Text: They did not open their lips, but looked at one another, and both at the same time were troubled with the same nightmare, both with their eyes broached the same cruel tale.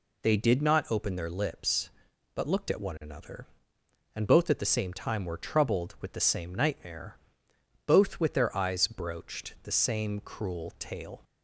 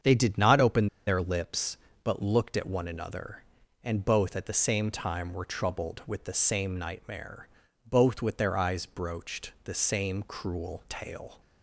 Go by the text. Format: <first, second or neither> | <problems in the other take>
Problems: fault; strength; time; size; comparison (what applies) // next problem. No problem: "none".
first | starts louder than the rest; strong; until 1.2 s; 7.5 dB // pauses between "open" and "their"; slight; at 0.8 s; 0.18 s long